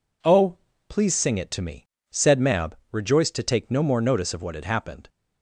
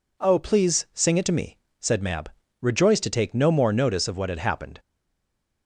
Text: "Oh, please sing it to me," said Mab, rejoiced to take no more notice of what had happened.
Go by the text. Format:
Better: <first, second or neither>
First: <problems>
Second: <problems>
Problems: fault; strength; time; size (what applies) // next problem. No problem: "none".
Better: first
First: none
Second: stays silent after the last word; slight; from 4.7 s on; 0.9 s long